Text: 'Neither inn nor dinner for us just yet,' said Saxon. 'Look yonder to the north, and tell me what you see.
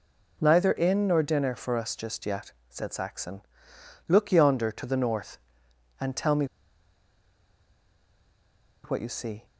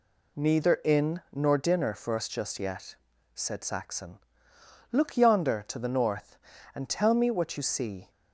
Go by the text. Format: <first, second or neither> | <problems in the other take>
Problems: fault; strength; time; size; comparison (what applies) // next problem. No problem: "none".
second | pauses between "me" and "what"; strong; at 6.4 s; 2.3 s long